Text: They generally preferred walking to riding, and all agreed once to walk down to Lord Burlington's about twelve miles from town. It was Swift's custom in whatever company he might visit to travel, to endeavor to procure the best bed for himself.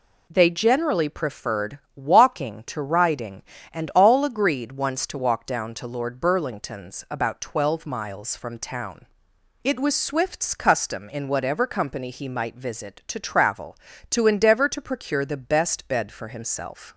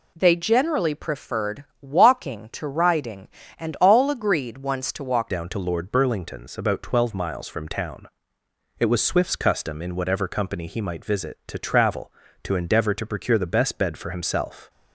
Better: first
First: pauses between "preferred" and "walking"; slight; at 1.7 s; 0.16 s long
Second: pauses between "preferred" and "walking"; slight; at 1.6 s; 0.16 s long // changes voice at "down"; from 5.2 s on; 9.4 s long

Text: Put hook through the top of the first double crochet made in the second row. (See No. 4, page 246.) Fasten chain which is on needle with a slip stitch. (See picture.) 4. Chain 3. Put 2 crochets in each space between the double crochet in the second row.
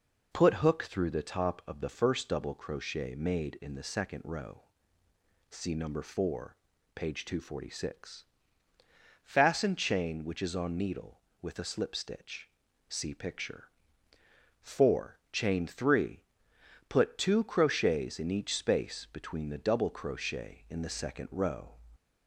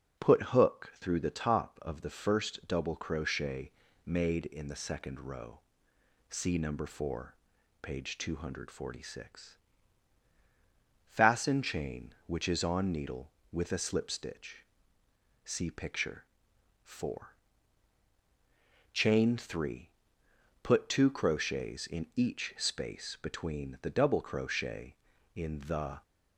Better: first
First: none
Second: pauses between "crochet" and "made"; slight; at 3.7 s; 0.34 s long // stops before "second row"; at 26.0 s

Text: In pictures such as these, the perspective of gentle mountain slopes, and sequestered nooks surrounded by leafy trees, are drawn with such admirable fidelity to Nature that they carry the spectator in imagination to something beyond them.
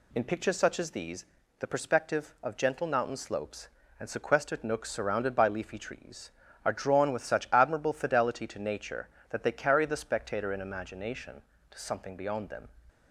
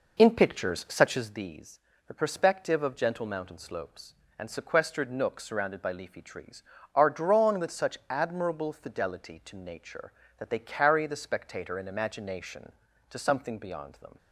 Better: first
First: none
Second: starts louder than the rest; noticeable; until 1.5 s; 4.5 dB

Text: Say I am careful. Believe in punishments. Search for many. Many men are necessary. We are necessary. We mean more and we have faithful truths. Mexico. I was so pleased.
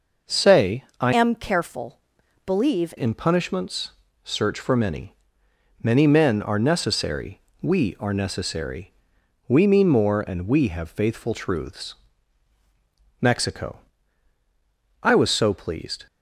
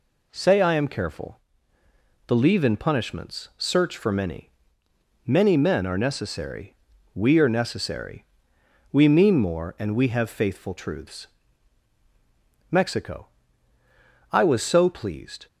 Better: second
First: pauses between "Say" and "I"; slight; at 0.8 s; 0.16 s long // changes voice from "am" to "Believe"; from 1.1 to 2.9 s; 1.8 s long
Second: none

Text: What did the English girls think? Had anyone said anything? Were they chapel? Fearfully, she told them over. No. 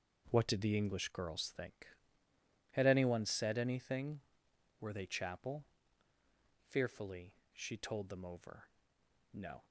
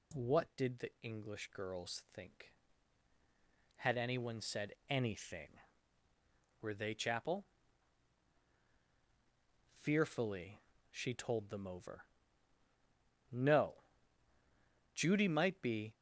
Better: first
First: none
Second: pauses between "said" and "anything"; slight; at 4.7 s; 0.16 s long // goes on to say "Judy might be"; noticeable; from 14.9 s on; 1.0 s long

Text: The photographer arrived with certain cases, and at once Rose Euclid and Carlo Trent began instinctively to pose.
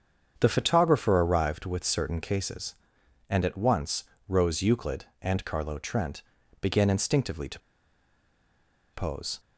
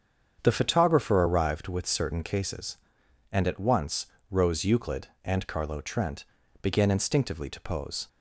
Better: second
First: starts louder than the rest; strong; until 1.3 s; 7.5 dB // pauses between "once" and "Rose"; slight; at 4.0 s; 0.26 s long // pauses between "Trent" and "began"; at 6.2 s; 0.40 s long // pauses between "to" and "pose"; strong; at 7.5 s; 1.3 s long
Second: starts louder than the rest; strong; until 1.4 s; 7.5 dB // pauses between "once" and "Rose"; slight; at 4.0 s; 0.26 s long // pauses between "Trent" and "began"; at 6.2 s; 0.38 s long

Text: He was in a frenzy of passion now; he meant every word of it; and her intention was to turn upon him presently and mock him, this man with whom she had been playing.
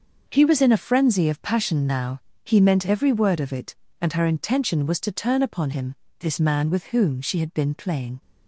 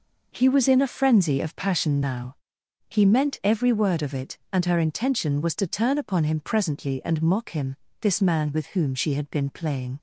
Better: second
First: starts louder than the rest; until 1.2 s; 6.5 dB // skips "him presently and mock"; at 5.7 s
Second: none

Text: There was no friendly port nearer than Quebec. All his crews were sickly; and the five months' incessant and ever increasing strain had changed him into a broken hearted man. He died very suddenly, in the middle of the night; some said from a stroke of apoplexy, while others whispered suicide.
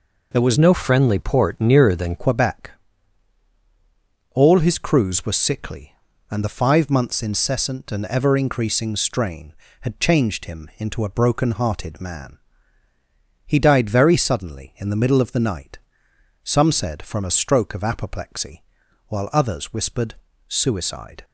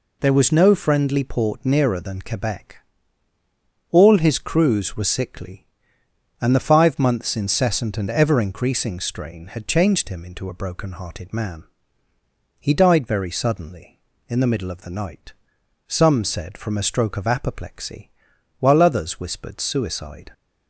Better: second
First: changes voice from "no" to "than"; from 0.5 to 2.1 s; 1.6 s long // pauses between "whispered" and "suicide"; slight; at 20.1 s; 0.34 s long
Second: none

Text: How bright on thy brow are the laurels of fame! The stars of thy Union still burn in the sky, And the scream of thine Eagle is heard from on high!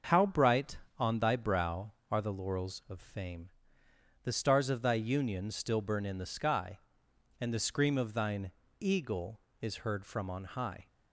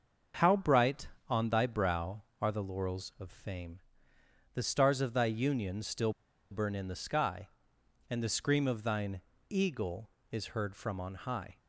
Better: first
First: starts louder than the rest; until 1.3 s; 7 dB // pauses between "thine" and "Eagle"; slight; at 8.4 s; 0.32 s long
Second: starts louder than the rest; until 1.6 s; 7 dB // pauses between "still" and "burn"; at 6.1 s; 0.39 s long // pauses between "thine" and "Eagle"; slight; at 9.1 s; 0.32 s long

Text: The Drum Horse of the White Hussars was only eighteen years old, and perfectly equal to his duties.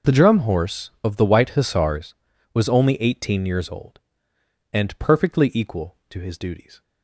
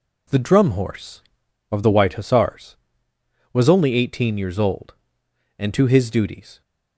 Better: first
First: none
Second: skips "perfectly equal"; at 5.7 s

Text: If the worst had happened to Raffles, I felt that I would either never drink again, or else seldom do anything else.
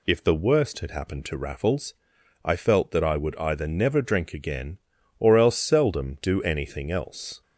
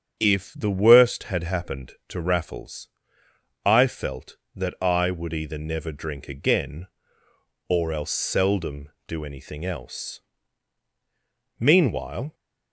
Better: first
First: none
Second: starts louder than the rest; strong; until 1.2 s; 7.5 dB // goes on to say "Meanwhile"; noticeable; from 11.5 s on; 0.76 s long

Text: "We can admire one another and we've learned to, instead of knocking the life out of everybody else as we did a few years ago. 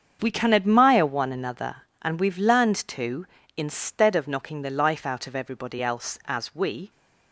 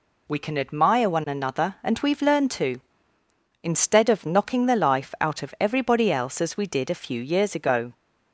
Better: second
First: starts louder than the rest; strong; until 1.2 s; 7 dB // stops before "did a few years ago"; at 6.8 s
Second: none

